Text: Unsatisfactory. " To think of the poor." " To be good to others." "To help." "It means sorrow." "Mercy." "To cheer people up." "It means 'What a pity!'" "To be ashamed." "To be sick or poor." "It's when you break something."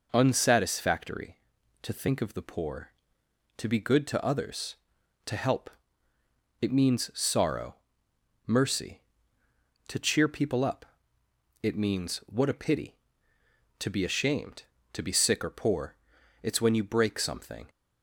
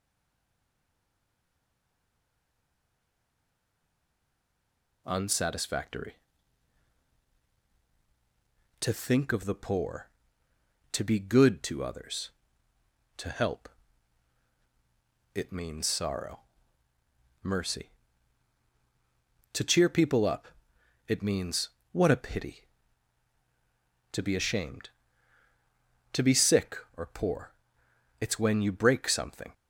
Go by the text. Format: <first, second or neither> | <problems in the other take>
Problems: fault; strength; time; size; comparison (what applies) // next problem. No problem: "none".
first | stays silent before the first word; strong; until 5.0 s; 5.0 s long // pauses between "means" and "What"; slight; at 21.6 s; 0.22 s long